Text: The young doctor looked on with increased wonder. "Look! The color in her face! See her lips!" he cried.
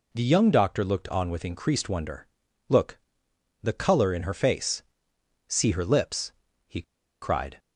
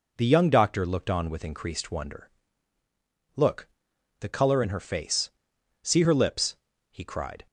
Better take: second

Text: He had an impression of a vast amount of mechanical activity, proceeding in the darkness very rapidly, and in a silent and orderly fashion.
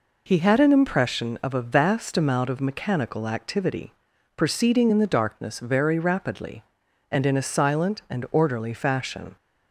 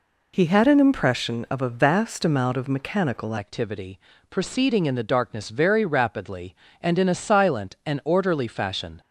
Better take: first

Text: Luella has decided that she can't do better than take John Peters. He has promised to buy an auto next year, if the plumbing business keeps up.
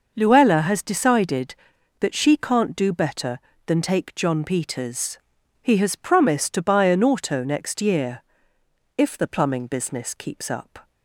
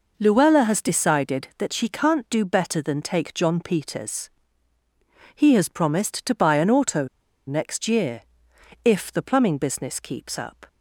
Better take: first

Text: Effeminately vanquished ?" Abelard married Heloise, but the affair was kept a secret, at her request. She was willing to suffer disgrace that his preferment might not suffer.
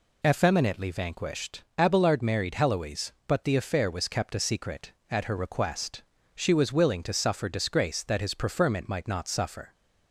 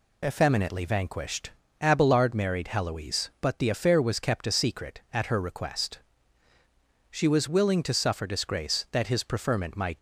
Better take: first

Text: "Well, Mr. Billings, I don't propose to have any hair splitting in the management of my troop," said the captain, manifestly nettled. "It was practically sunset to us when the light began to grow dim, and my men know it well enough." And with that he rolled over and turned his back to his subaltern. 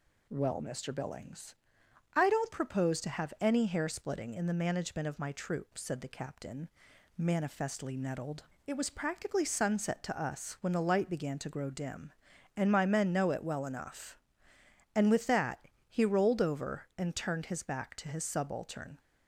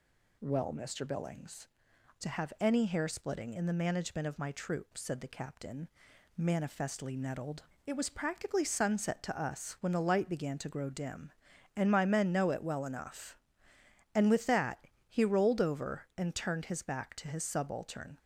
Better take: first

